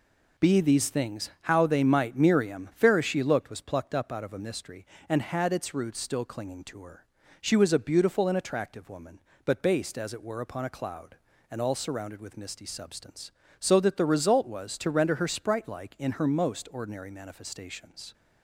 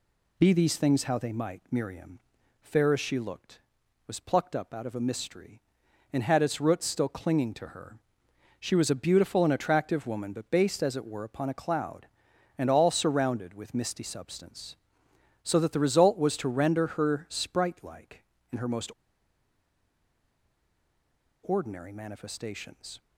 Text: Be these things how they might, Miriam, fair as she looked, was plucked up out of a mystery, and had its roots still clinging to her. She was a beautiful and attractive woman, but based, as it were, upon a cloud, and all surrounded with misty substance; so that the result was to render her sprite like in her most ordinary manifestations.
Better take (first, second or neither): first